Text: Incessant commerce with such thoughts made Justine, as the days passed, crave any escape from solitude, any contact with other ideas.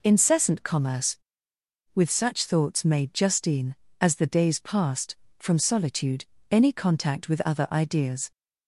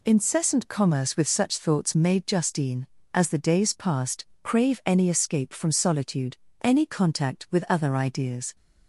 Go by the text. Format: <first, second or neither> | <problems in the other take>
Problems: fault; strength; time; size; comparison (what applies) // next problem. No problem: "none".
second | skips "crave any escape"; at 5.2 s